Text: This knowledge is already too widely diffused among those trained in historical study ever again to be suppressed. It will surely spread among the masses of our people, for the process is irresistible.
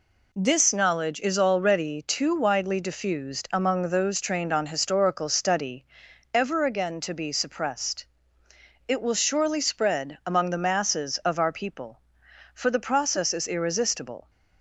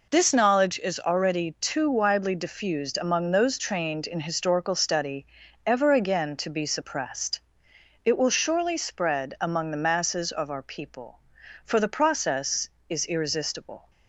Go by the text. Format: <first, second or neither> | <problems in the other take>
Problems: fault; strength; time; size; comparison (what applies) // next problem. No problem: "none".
second | says "on" for "in"; at 4.4 s // pauses between "study" and "ever"; noticeable; at 5.8 s; 0.50 s long; also in the second